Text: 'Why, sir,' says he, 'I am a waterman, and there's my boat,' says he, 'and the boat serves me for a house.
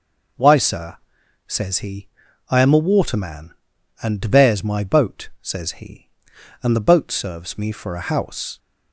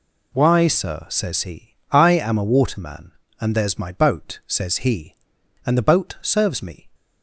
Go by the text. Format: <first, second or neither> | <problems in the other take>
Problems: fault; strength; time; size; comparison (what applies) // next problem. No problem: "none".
first | stops before "for a house"; at 6.9 s